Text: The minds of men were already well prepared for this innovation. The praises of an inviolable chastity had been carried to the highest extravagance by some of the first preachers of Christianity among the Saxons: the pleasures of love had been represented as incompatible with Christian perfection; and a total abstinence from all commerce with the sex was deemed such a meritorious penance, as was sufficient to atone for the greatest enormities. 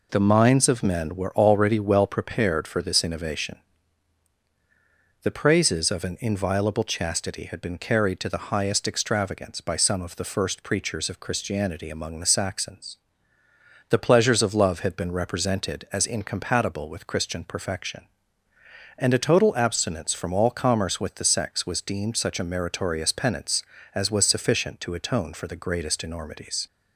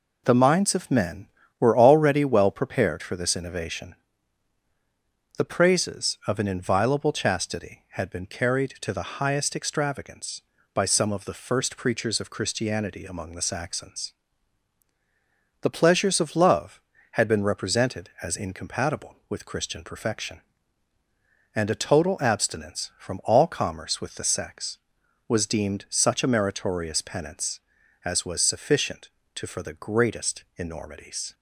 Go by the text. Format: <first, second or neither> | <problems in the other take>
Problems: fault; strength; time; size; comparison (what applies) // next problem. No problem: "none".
first | skips "atone"; at 29.4 s